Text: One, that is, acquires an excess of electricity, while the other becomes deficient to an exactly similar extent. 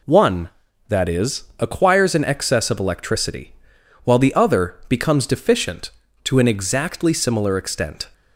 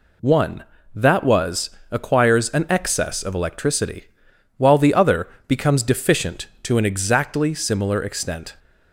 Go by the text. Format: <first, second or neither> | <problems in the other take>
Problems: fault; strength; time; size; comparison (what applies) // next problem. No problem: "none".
first | says "was" for "is"; at 1.2 s // pauses between "other" and "becomes"; slight; at 5.2 s; 0.20 s long